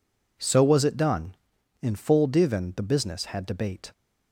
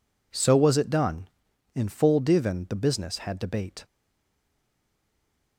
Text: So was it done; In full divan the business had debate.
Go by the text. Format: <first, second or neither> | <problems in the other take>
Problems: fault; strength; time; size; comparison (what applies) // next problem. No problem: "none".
first | stays silent after the last word; noticeable; from 3.8 s on; 1.7 s long